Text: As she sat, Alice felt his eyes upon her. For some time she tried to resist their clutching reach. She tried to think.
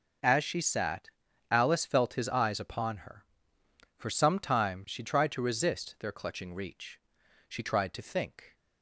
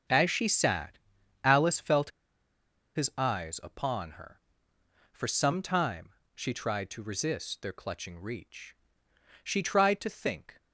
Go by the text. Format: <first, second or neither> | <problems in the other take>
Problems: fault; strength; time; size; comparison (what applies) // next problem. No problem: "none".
first | starts louder than the rest; noticeable; until 1.5 s; 6 dB // pauses between "felt" and "his"; noticeable; at 2.1 s; 0.85 s long // pauses between "time" and "she"; slight; at 6.0 s; 0.24 s long